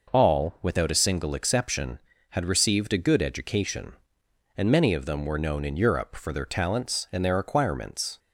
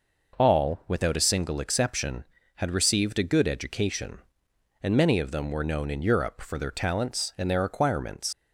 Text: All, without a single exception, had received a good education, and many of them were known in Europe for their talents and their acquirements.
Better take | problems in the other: first | leaves "acquirements" unfinished; at 8.3 s; 115 ms

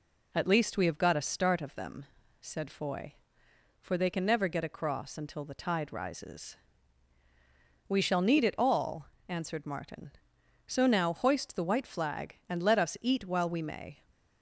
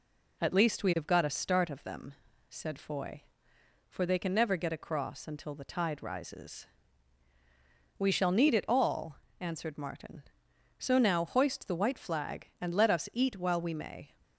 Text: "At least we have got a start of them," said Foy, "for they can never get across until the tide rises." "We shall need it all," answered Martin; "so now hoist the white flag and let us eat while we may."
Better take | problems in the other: neither | none

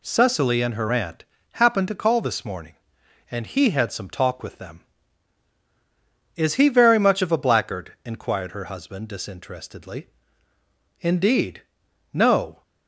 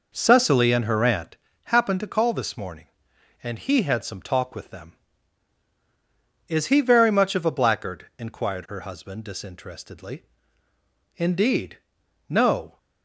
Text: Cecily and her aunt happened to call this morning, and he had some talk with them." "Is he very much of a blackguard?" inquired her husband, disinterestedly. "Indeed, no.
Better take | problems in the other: first | starts louder than the rest; noticeable; until 1.3 s; 5 dB // pauses between "aunt" and "happened"; slight; at 1.3 s; 0.28 s long; slight in the first

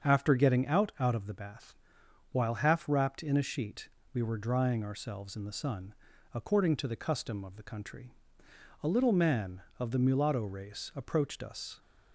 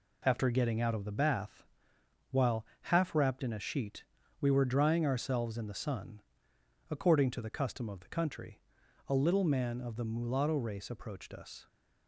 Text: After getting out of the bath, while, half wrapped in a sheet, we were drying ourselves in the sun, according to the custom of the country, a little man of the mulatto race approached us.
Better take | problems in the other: second | starts louder than the rest; until 1.1 s; 7 dB // says "out" twice; at 1.0 s

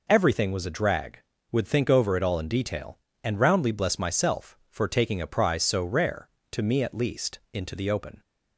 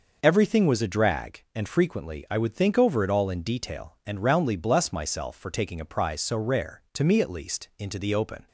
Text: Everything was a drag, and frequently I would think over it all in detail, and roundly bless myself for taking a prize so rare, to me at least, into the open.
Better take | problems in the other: second | skips "and frequently I"; at 1.3 s

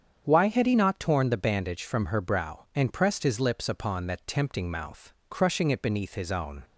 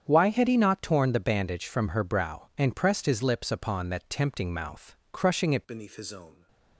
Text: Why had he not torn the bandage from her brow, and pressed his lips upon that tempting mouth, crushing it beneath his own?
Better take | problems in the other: first | starts louder than the rest; strong; until 1.1 s; 8.5 dB; strong in the first // changes voice at "beneath"; from 5.6 s on; 0.8 s long

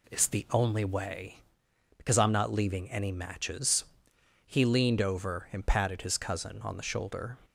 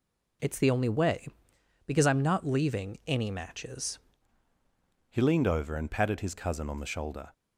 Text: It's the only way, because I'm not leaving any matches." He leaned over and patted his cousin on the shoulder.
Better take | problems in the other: first | changes voice at "He"; from 5.0 s on; 2.3 s long

